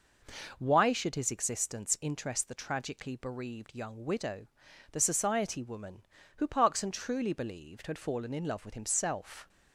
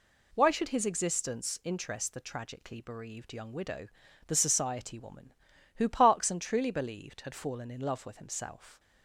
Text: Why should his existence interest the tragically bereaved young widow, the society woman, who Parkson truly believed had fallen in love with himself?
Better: neither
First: none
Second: none

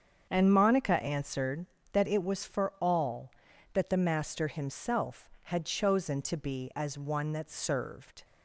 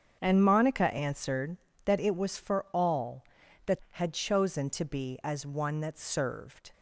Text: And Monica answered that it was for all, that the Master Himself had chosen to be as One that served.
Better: first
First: starts louder than the rest; strong; until 1.3 s; 7.5 dB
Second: starts louder than the rest; strong; until 1.2 s; 7.5 dB // skips "the Master Himself"; at 3.8 s

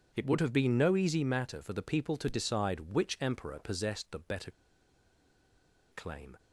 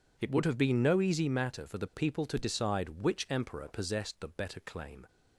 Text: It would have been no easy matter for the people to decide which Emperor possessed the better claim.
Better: second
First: pauses between "better" and "claim"; strong; at 4.5 s; 1.4 s long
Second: none

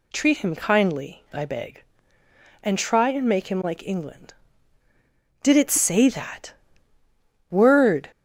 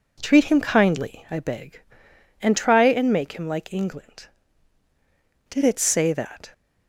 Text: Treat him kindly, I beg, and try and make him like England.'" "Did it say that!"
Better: second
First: goes on to say "Word"; from 7.5 s on; 0.58 s long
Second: none

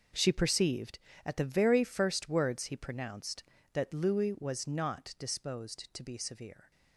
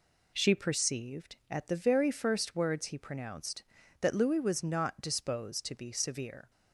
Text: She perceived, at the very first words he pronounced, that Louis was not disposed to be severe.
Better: second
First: gets quieter; strong; throughout; 14 dB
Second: none

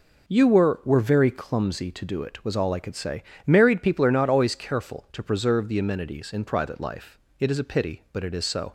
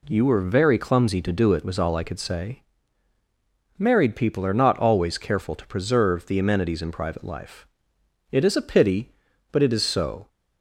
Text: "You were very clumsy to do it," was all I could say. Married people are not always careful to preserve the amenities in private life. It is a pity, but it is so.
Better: second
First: says "were" twice; at 0.8 s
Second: none

